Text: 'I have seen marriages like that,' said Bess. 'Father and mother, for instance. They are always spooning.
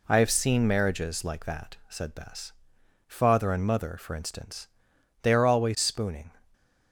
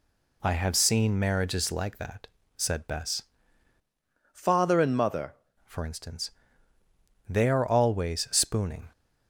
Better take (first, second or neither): first